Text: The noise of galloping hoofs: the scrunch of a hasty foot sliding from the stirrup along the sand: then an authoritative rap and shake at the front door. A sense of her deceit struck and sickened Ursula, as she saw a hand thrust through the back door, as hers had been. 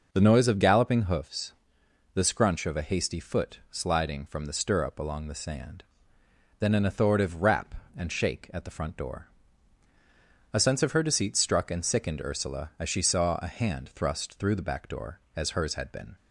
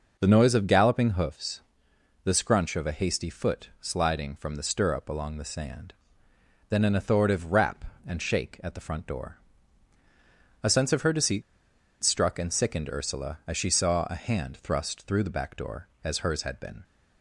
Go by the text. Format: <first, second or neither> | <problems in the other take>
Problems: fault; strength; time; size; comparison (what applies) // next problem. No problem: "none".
first | pauses between "deceit" and "struck"; noticeable; at 11.4 s; 0.60 s long